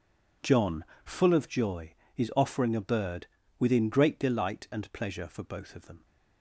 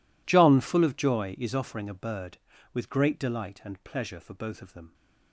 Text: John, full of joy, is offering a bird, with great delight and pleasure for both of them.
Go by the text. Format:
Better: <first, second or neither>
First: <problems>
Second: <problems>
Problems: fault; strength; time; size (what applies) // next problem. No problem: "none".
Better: second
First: says "within" for "with"; at 3.5 s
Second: none